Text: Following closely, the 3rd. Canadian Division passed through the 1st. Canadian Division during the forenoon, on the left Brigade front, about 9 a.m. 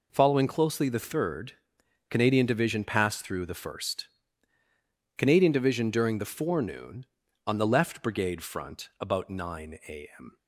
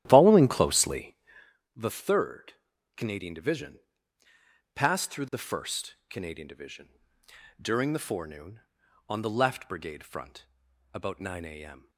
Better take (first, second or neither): first